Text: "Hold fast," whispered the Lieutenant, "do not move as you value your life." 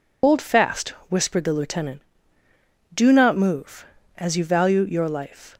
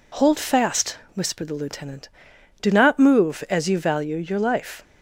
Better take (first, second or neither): second